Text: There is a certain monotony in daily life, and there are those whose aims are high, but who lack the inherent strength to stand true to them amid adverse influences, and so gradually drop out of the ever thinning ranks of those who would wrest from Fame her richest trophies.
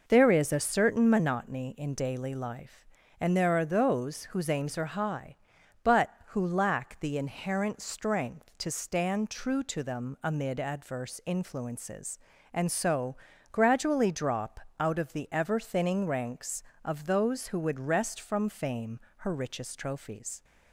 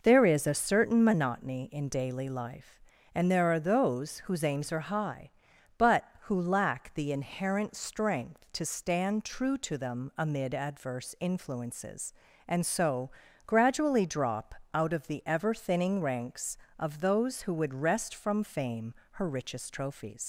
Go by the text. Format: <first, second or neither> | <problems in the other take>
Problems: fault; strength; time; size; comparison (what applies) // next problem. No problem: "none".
first | pauses between "so" and "gradually"; slight; at 13.1 s; 0.36 s long; slight in the first // pauses between "drop" and "out"; slight; at 14.5 s; 0.18 s long; slight in the first // pauses between "Fame" and "her"; slight; at 18.9 s; 0.18 s long; slight in the first // leaves "trophies" unfinished; at 20.2 s; 100 ms